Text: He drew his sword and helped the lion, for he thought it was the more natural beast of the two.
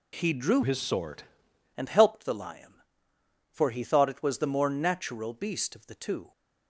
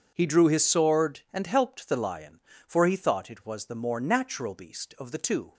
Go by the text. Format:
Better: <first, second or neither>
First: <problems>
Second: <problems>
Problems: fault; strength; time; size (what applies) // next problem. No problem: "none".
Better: second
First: changes voice from "his" to "sword"; from 0.6 to 1.2 s; 0.6 s long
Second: none